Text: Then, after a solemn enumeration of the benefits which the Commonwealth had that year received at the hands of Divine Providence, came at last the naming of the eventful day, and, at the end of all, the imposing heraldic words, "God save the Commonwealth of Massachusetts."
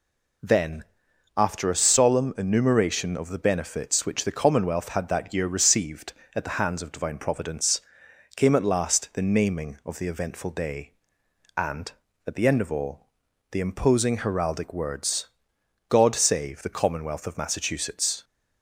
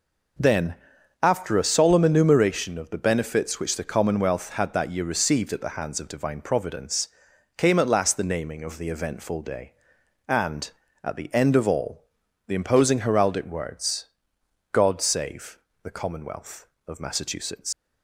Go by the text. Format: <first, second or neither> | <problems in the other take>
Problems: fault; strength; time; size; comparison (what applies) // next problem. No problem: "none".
first | pauses between "save" and "the"; slight; at 15.5 s; 0.26 s long // leaves "Massachusetts" unfinished; at 17.7 s; 105 ms